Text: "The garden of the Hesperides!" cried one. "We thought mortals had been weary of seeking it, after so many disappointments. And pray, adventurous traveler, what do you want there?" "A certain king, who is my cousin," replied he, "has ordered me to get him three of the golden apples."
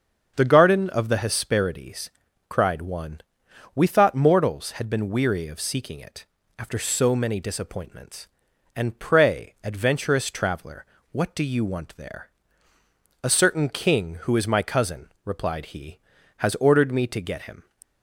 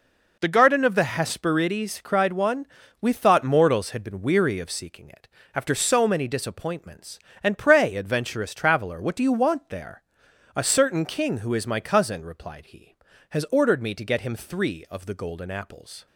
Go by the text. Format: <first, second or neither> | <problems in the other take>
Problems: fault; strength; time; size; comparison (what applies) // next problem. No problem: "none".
second | starts louder than the rest; until 1.3 s; 6.5 dB // stops before "three of the golden apples"; at 17.8 s